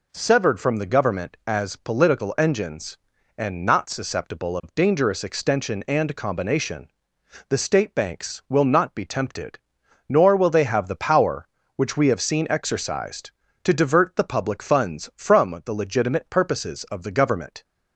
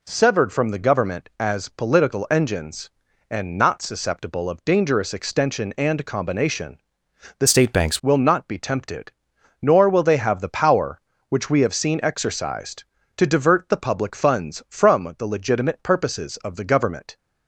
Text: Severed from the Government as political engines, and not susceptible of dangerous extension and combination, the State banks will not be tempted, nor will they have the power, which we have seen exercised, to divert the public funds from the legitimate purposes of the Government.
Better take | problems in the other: first | changes voice from "State" to "banks"; from 7.4 to 7.9 s; 0.5 s long

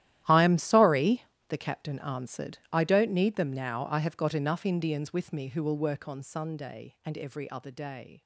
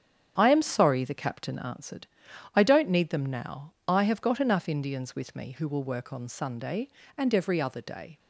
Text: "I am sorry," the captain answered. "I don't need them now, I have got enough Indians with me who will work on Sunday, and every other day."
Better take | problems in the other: second | gets quieter; strong; throughout; 16.5 dB // starts louder than the rest; strong; until 1.5 s; 13 dB; strong in the second

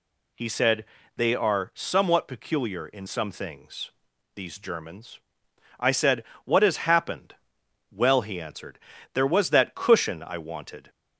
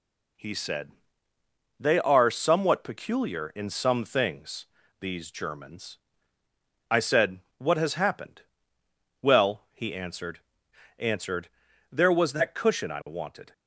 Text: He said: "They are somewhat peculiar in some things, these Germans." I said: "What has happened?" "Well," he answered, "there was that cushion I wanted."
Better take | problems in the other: first | says "answered" twice; at 10.9 s

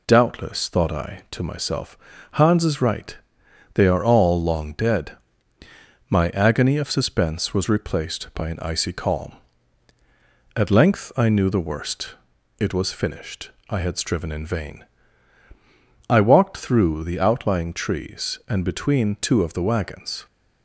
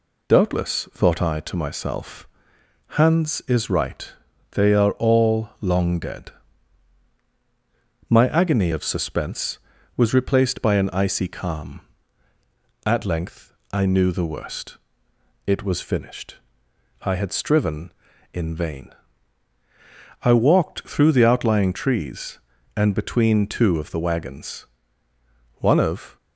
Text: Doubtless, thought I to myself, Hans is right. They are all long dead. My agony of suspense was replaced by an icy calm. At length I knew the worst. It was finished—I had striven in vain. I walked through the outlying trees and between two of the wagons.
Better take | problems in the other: first | pauses between "length" and "I"; slight; at 13.5 s; 0.18 s long // goes on to say "One of"; from 25.5 s on; 0.58 s long

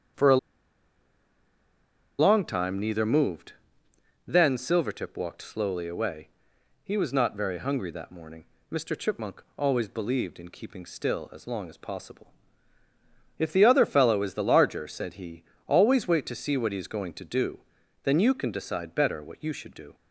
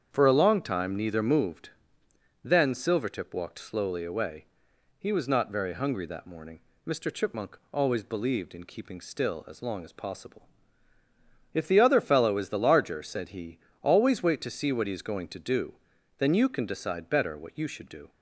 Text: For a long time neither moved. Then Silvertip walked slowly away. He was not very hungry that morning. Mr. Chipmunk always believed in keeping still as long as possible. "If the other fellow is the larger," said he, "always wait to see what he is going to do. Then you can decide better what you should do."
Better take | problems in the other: second | starts louder than the rest; strong; until 2.9 s; 7.5 dB; strong in the second // pauses between "a" and "long"; strong; at 0.3 s; 1.8 s long

